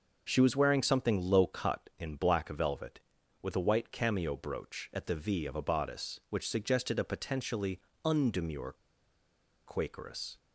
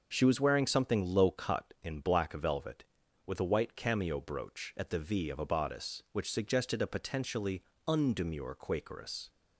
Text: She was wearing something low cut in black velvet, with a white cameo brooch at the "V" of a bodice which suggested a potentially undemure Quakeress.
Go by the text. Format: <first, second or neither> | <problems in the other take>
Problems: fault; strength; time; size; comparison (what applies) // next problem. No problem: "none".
second | starts louder than the rest; noticeable; until 1.2 s; 6 dB; noticeable in the second // pauses between "potentially" and "undemure"; slight; at 7.7 s; 0.24 s long; slight in the second // pauses between "undemure" and "Quakeress"; noticeable; at 8.7 s; 0.90 s long